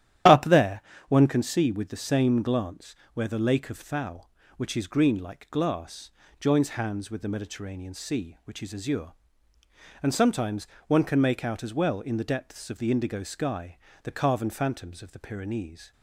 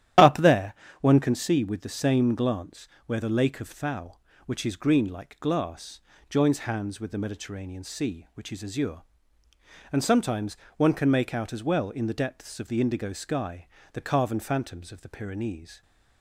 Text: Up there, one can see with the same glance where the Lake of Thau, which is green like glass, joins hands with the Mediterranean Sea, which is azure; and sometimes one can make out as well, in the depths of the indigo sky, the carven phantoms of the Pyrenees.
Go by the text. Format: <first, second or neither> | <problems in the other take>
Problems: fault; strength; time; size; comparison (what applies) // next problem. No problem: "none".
neither | starts louder than the rest; strong; the same in both // pauses between "glance" and "where"; slight; the same in both // pauses between "sometimes" and "one"; slight; the same in both